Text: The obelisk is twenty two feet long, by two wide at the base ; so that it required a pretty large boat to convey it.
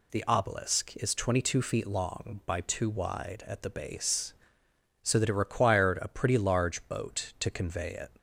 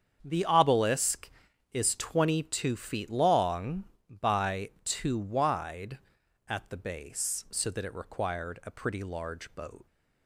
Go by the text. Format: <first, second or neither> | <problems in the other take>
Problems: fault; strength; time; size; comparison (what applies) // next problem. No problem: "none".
first | starts louder than the rest; strong; until 1.2 s; 7.5 dB // pauses between "by" and "two"; slight; at 4.6 s; 0.16 s long // stops before "to convey it"; at 9.8 s